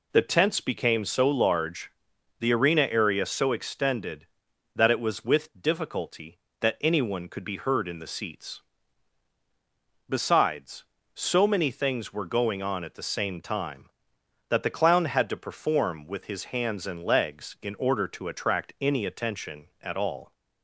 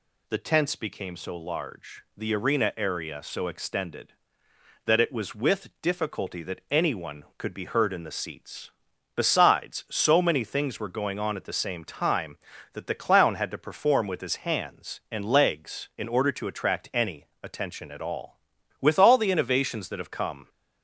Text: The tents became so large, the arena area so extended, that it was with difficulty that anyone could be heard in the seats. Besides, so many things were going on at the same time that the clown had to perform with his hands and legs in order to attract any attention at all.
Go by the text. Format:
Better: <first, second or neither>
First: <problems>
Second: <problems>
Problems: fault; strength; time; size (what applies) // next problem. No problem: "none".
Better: first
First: none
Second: pauses between "any" and "attention"; slight; at 17.2 s; 0.16 s long // goes on to say "With all the innovations that have come"; strong; from 18.8 s on; 1.6 s long